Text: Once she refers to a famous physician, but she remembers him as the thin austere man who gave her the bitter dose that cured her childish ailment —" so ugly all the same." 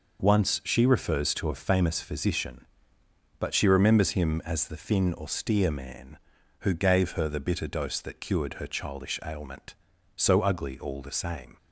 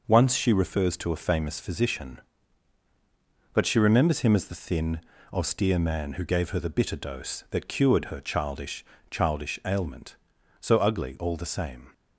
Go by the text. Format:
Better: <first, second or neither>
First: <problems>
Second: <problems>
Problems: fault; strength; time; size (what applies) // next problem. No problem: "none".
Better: first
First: none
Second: pauses between "thin" and "austere"; slight; at 4.9 s; 0.34 s long // says "childish" twice; at 9.1 s